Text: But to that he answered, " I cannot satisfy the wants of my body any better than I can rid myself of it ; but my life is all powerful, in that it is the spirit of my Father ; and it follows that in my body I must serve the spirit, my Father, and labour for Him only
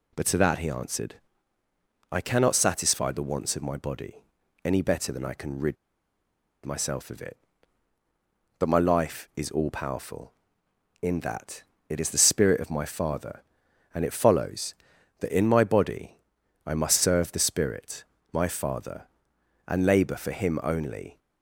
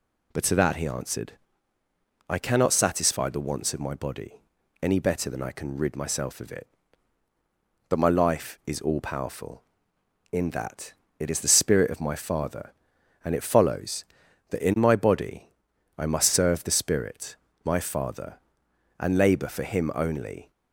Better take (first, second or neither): second